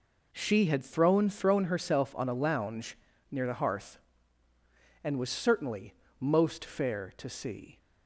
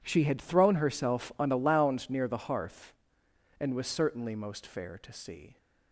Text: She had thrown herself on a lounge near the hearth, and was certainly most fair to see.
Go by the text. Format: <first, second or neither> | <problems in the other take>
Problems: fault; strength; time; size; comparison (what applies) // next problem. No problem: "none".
second | says "thrown" twice; at 1.2 s // pauses between "lounge" and "near"; slight; at 2.9 s; 0.34 s long // pauses between "certainly" and "most"; slight; at 5.9 s; 0.28 s long